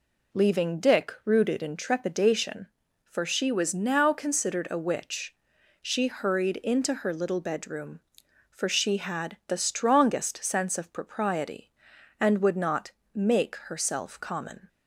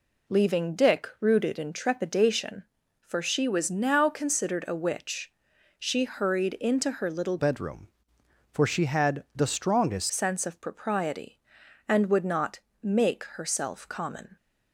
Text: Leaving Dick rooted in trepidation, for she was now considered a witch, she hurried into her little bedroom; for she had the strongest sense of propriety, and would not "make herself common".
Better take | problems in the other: first | changes voice from "bedroom" to "strongest"; from 7.3 to 10.0 s; 2.7 s long // pauses between "not" and "make"; slight; at 12.5 s; 0.22 s long; slight in the first

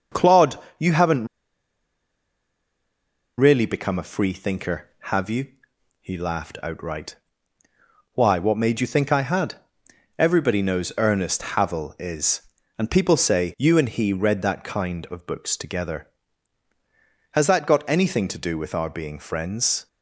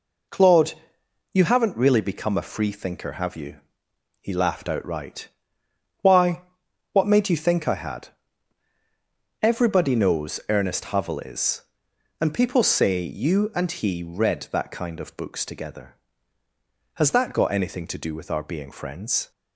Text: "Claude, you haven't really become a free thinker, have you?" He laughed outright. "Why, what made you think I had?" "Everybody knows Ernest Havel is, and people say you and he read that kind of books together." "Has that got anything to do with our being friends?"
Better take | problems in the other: second | starts louder than the rest; noticeable; until 3.4 s; 6 dB // pauses between "haven't" and "really"; strong; at 1.2 s; 2.1 s long

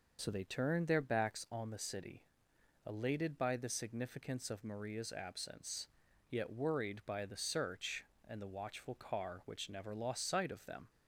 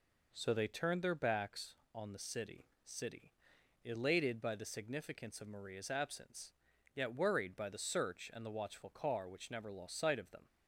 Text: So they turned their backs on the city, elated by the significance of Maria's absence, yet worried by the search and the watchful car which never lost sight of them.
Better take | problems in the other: first | says "city" twice; at 2.8 s

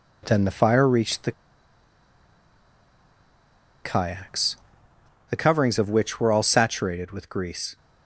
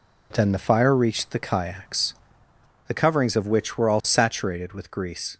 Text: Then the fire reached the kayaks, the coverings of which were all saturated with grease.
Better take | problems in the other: second | pauses between "the" and "kayaks"; strong; at 1.3 s; 2.5 s long

